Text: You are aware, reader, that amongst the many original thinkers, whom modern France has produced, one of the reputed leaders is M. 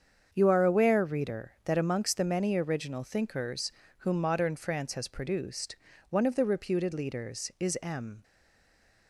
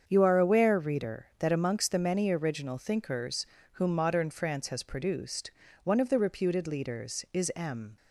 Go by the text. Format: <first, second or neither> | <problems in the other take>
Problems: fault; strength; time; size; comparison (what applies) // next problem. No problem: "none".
second | starts louder than the rest; strong; until 1.3 s; 7.5 dB; strong in the second // stays silent after the last word; slight; from 8.2 s on; 0.8 s long